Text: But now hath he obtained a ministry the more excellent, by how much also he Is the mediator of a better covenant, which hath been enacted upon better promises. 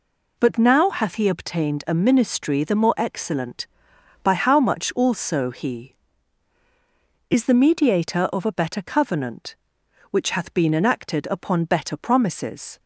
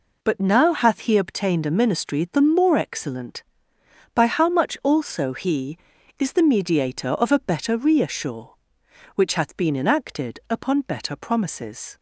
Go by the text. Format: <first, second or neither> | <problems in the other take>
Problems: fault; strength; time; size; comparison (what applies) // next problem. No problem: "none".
first | says "reassure" for "covenant"; at 7.7 s